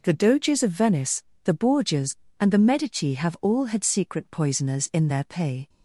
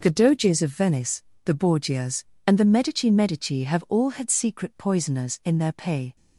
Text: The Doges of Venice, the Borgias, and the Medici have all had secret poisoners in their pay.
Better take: first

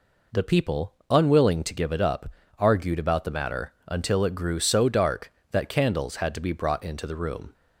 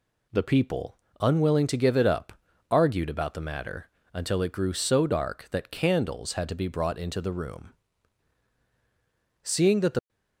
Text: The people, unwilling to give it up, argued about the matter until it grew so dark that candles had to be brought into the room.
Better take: first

